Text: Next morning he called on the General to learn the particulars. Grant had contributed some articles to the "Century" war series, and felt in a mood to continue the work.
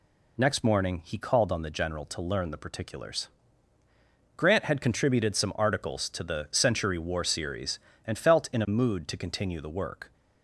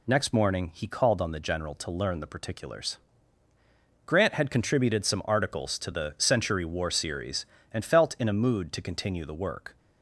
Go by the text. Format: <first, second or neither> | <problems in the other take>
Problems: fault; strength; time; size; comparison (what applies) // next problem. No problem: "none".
neither | none